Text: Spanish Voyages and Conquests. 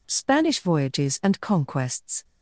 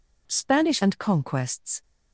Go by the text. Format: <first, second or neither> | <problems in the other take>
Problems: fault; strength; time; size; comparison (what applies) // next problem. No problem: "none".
first | skips "Voyages"; at 0.7 s